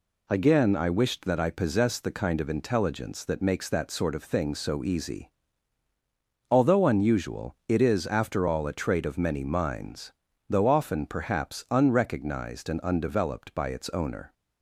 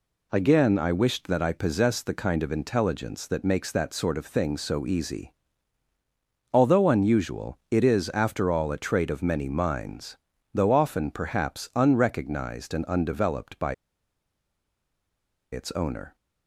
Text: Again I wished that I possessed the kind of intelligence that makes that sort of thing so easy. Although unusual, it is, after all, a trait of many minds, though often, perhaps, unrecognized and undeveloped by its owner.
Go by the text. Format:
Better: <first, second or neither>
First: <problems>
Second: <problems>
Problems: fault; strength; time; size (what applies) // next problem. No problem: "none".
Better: first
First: none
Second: pauses between "by" and "its"; strong; at 13.7 s; 1.7 s long